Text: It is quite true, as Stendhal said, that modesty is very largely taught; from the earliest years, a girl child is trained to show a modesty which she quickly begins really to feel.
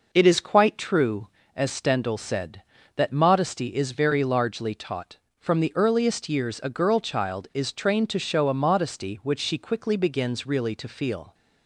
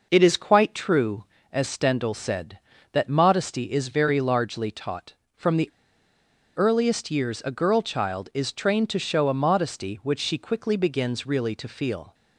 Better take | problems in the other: first | pauses between "the" and "earliest"; noticeable; at 5.6 s; 0.87 s long

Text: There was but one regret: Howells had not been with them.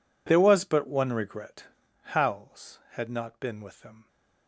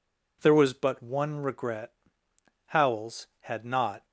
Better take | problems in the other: first | stops before "been with them"; at 4.0 s

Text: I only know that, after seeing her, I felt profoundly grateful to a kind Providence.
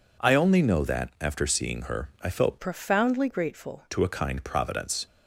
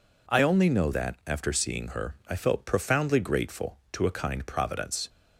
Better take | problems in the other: second | changes voice from "profoundly" to "grateful"; from 2.6 to 3.8 s; 1.2 s long

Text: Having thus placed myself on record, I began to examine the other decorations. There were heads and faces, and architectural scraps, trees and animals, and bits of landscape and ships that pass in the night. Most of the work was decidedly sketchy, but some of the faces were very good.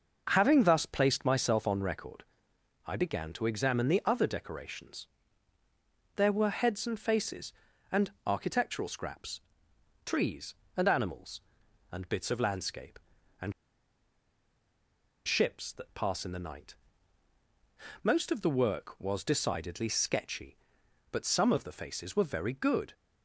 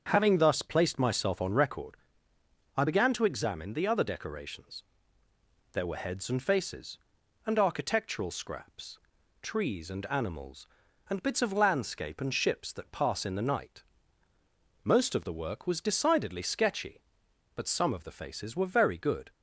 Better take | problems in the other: second | starts louder than the rest; noticeable; until 1.3 s; 6 dB; also in the second // pauses between "and" and "architectural"; slight; at 8.0 s; 0.16 s long // pauses between "and" and "ships"; strong; at 13.5 s; 1.7 s long

